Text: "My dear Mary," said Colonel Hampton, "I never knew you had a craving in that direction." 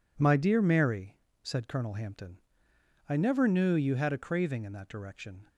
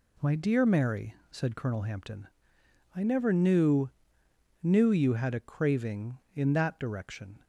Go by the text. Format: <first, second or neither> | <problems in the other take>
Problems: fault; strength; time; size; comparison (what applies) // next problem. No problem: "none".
first | says "knew" twice; at 4.6 s